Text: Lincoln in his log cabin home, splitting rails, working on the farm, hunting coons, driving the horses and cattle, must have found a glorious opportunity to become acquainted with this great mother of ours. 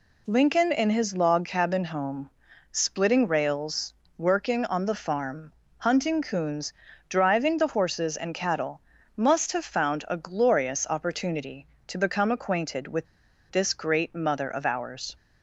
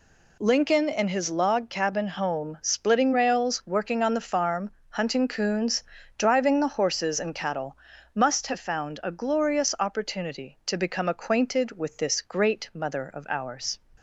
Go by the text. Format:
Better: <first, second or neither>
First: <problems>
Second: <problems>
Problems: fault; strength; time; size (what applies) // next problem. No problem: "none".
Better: second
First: pauses between "with" and "this"; noticeable; at 13.0 s; 0.47 s long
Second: none